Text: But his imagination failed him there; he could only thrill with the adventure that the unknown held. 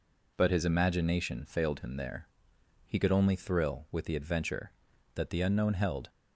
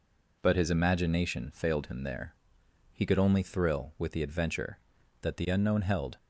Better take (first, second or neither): neither